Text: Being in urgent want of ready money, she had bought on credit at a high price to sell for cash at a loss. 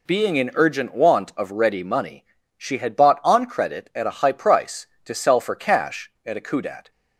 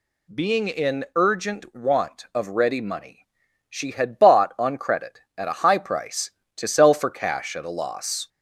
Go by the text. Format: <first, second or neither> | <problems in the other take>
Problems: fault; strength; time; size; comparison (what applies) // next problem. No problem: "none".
second | says "kudat" for "loss"; at 6.4 s